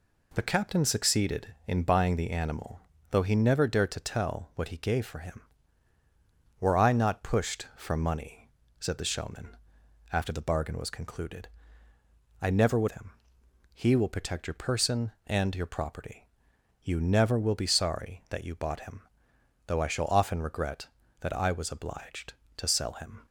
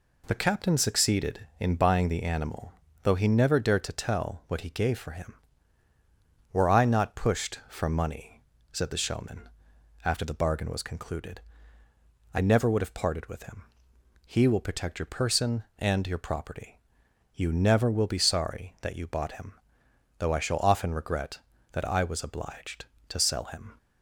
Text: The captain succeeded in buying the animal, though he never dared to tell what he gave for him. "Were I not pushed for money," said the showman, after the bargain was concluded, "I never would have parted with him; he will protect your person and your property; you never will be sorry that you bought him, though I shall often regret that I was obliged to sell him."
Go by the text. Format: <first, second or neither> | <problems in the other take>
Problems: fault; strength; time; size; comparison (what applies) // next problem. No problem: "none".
second | skips "have parted with"; at 12.8 s